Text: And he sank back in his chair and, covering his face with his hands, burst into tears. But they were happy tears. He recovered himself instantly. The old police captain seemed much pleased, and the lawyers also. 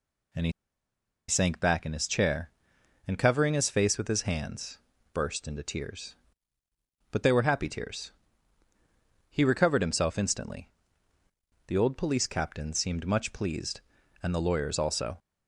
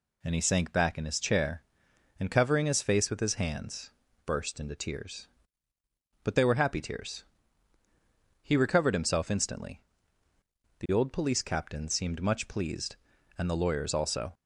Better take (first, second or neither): second